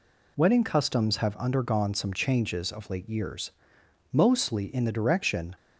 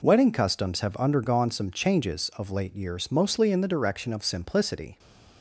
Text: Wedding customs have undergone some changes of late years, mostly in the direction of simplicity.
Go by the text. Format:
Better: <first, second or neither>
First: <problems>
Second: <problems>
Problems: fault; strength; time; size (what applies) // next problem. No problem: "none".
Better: second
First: stops before "of simplicity"; at 5.5 s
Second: none